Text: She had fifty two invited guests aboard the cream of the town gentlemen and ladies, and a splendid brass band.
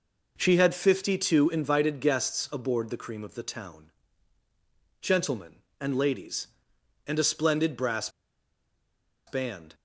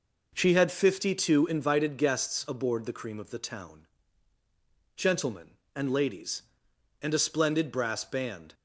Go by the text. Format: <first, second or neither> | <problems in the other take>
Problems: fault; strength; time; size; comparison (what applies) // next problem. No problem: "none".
second | pauses between "town" and "gentlemen"; at 3.9 s; 1.1 s long; also in the second // pauses between "brass" and "band"; at 8.0 s; 1.1 s long